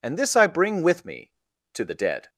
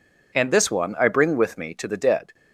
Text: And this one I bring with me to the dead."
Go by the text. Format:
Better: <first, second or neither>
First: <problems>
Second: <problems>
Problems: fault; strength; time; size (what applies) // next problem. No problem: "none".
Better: second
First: skips "one"; at 0.3 s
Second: none